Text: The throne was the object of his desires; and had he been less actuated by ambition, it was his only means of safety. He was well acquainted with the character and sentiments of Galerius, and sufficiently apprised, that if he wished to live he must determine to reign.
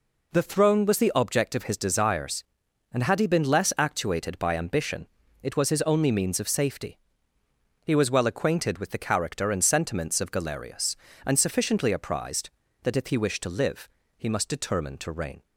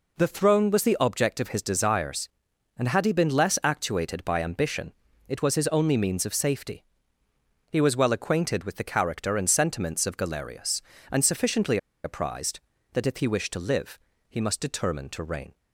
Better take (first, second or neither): first